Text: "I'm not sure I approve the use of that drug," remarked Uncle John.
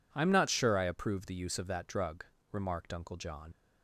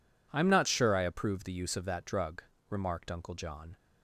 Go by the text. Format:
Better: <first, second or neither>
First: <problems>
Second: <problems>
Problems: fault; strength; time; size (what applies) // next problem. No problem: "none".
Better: second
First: leaves "John" unfinished; at 3.5 s; 75 ms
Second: none